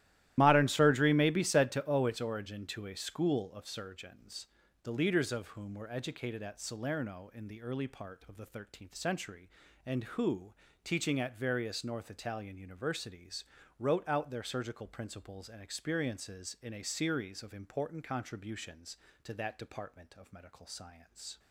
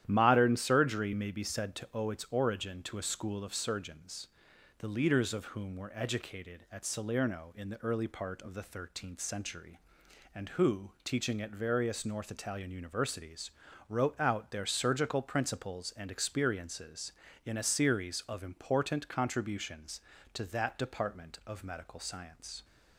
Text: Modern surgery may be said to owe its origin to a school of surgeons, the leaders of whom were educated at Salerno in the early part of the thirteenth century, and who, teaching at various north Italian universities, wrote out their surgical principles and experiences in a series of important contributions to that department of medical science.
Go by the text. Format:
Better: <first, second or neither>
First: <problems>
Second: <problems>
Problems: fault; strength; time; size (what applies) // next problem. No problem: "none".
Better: second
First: loses the start of "Modern"; at 0.3 s; 35 ms // starts louder than the rest; strong; until 1.3 s; 14.5 dB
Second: starts louder than the rest; strong; until 1.0 s; 11.5 dB